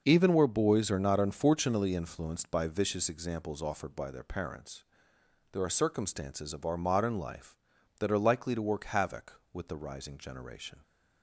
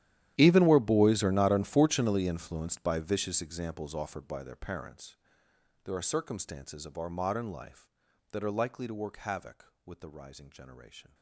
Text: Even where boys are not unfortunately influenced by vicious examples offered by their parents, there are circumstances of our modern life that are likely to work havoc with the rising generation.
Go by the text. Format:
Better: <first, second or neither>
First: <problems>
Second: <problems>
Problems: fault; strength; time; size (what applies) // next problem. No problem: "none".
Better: first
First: none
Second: gets quieter; strong; throughout; 21 dB